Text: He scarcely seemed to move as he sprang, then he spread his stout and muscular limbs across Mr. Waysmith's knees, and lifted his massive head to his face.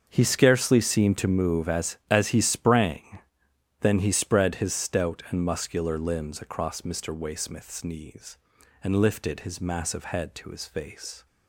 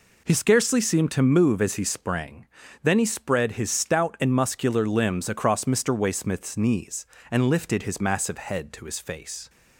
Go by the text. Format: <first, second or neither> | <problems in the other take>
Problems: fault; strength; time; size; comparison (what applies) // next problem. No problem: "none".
second | starts louder than the rest; until 1.0 s; 6.5 dB // says "as" twice; at 2.0 s